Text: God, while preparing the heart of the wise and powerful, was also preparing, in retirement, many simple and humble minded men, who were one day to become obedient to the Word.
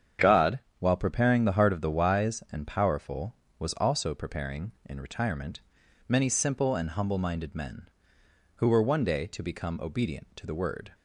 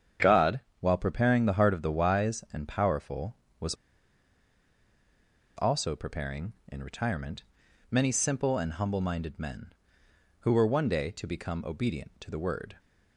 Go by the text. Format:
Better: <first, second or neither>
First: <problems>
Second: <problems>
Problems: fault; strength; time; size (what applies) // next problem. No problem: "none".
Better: first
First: starts louder than the rest; strong; until 1.4 s; 8 dB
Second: starts louder than the rest; strong; until 1.4 s; 8 dB // pauses between "was" and "also"; strong; at 3.7 s; 1.8 s long